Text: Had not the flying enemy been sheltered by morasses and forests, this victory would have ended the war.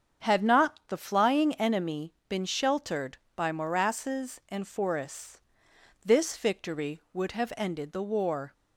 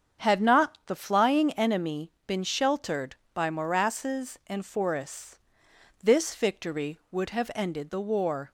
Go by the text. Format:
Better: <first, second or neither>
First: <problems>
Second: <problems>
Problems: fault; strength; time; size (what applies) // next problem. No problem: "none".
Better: neither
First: starts louder than the rest; strong; until 1.3 s; 7.5 dB // pauses between "enemy" and "been"; slight; at 2.1 s; 0.16 s long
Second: starts louder than the rest; strong; until 1.3 s; 7.5 dB // pauses between "enemy" and "been"; slight; at 2.1 s; 0.16 s long